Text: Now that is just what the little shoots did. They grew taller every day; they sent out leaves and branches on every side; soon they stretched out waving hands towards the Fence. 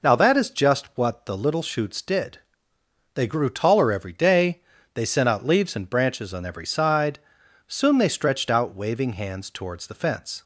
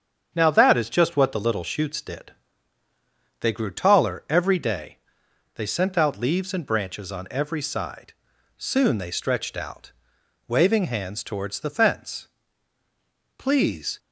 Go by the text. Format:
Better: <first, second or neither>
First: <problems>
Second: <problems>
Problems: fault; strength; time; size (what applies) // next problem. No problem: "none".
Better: first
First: none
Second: starts louder than the rest; strong; until 1.3 s; 7.5 dB // pauses between "out" and "waving"; noticeable; at 9.9 s; 0.56 s long // goes on to say "Please"; from 13.3 s on; 0.60 s long